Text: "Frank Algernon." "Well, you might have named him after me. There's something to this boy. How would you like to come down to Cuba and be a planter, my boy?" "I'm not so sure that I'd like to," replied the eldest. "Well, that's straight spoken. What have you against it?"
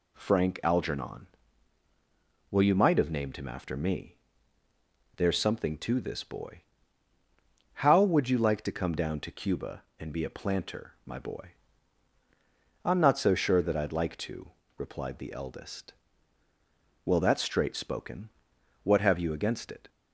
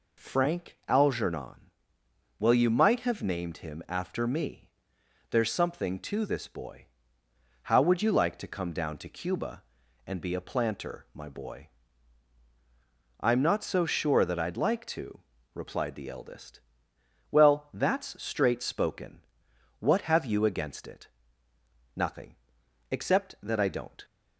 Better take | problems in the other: first | goes on to say "Nothing except that I don't"; strong; from 21.9 s on; 2.1 s long

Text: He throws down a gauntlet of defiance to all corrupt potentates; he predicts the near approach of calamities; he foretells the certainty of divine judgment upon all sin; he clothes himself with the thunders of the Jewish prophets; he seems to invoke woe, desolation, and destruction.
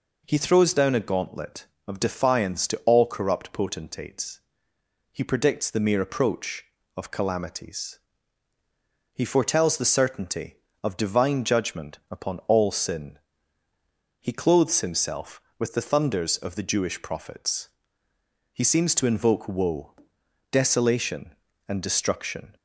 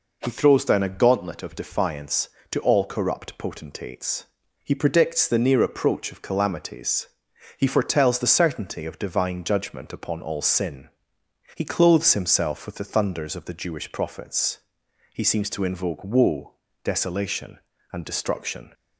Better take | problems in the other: second | says "mere" for "near"; at 5.8 s

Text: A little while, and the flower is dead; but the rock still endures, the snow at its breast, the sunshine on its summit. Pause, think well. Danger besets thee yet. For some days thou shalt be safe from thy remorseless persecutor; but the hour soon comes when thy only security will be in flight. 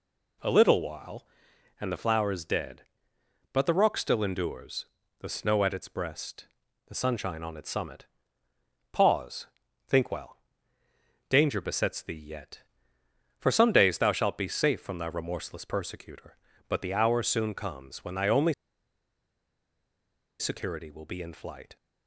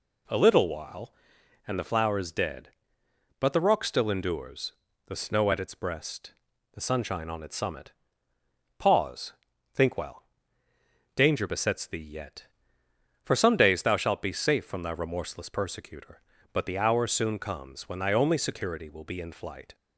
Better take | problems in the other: second | pauses between "only" and "security"; strong; at 18.5 s; 1.8 s long

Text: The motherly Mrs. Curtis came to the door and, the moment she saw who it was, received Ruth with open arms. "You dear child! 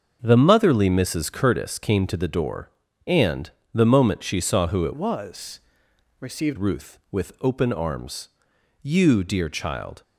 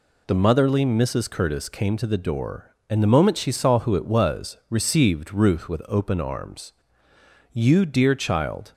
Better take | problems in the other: second | starts louder than the rest; until 1.2 s; 6.5 dB // changes voice from "was" to "received"; from 4.9 to 6.5 s; 1.6 s long

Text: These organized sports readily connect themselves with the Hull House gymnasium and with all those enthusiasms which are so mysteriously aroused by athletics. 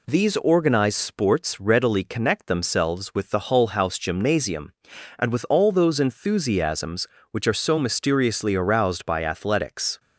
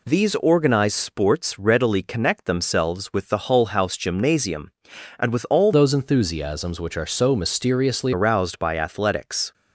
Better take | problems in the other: first | changes voice from "those" to "mysteriously"; from 5.7 to 8.1 s; 2.4 s long

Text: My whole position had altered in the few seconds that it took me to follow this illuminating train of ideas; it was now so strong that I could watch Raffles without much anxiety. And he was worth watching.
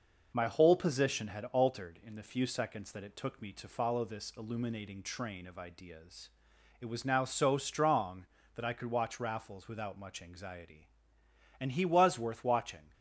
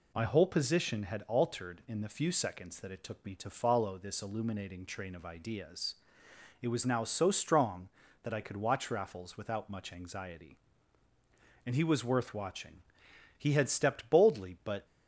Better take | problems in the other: first | goes on to say "He had stepped boldly but"; from 13.3 s on; 1.4 s long

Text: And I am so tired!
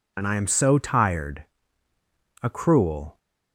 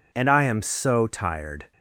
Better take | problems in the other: second | goes on to say "A cruel"; noticeable; from 2.4 s on; 0.76 s long

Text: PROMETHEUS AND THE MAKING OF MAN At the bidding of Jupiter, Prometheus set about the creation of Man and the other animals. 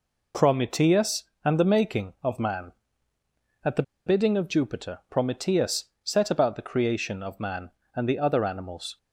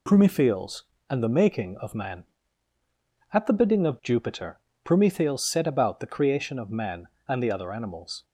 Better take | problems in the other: second | pauses between "the" and "bidding"; slight; at 3.8 s; 0.24 s long // pauses between "Prometheus" and "set"; slight; at 5.8 s; 0.18 s long

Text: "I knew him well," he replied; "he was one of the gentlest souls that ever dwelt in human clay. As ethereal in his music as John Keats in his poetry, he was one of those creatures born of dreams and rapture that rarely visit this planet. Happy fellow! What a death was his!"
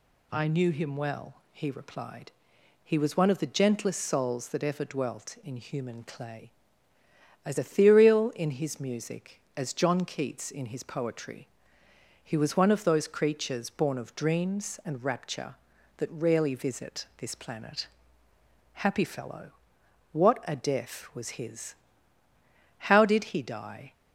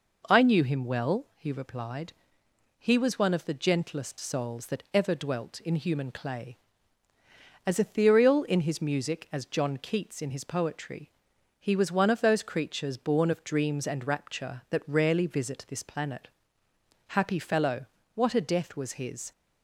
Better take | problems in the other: second | goes on to say "How did he die"; noticeable; from 22.7 s on; 1.1 s long

